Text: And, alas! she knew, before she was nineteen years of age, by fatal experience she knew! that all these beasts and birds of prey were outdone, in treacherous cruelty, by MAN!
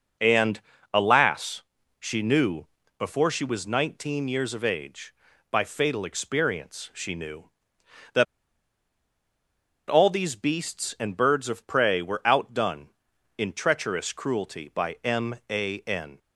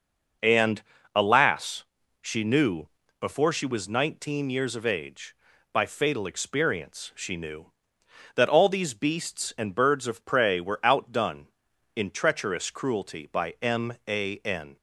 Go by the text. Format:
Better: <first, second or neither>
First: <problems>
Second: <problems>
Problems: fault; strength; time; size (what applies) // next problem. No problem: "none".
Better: second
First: pauses between "that" and "all"; strong; at 8.2 s; 1.6 s long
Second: none